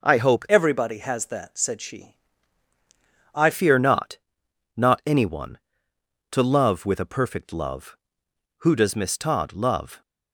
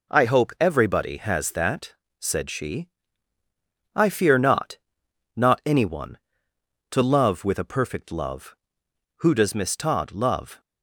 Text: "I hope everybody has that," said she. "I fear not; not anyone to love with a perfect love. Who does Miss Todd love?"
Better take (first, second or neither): second